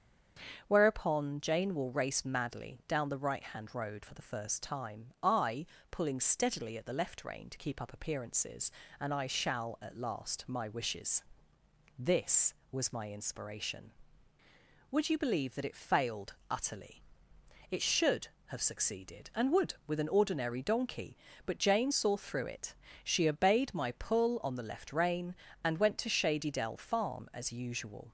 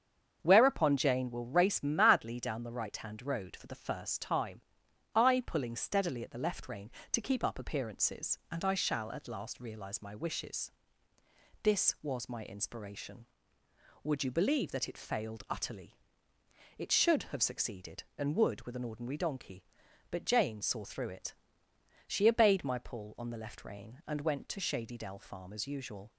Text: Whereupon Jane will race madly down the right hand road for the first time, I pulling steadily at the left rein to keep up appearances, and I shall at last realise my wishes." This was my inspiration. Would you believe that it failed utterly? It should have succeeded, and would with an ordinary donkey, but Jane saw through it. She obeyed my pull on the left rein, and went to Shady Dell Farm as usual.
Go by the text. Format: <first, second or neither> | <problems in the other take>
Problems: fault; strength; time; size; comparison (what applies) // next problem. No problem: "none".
second | starts louder than the rest; strong; until 1.6 s; 7.5 dB; strong in the second // pauses between "I" and "pulling"; slight; at 5.6 s; 0.26 s long // skips "realise"; at 10.4 s